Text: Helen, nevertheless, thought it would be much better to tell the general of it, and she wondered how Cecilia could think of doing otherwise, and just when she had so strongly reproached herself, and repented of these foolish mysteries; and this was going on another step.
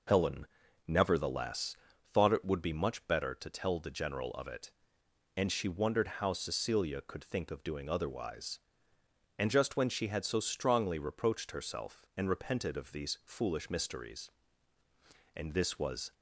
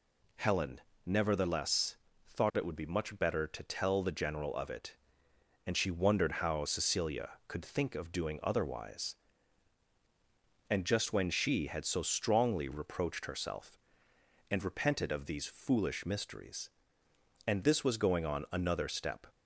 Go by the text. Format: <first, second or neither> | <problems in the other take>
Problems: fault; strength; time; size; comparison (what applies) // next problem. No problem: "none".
second | stops before "going on another step"; at 16.1 s